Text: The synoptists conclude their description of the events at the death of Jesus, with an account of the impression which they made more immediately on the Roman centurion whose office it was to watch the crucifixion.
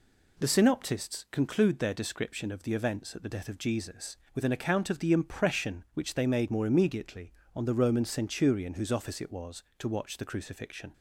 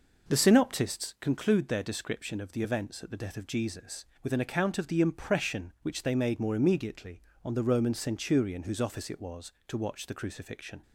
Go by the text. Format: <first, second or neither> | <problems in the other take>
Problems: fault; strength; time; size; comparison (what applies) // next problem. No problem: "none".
first | starts louder than the rest; noticeable; until 1.1 s; 5 dB